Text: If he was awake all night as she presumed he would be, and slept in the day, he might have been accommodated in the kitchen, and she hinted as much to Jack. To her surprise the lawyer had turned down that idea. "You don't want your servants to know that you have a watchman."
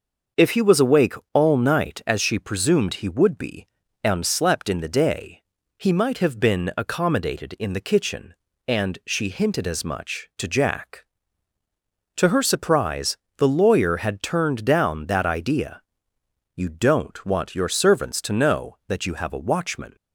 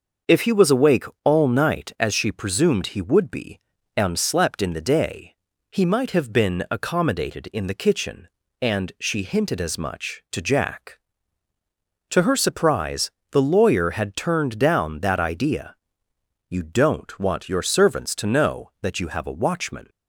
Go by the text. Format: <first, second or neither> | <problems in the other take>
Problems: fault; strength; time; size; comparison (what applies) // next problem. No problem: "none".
neither | starts louder than the rest; the same in both // pauses between "awake" and "all"; slight; the same in both // pauses between "surprise" and "the"; slight; the same in both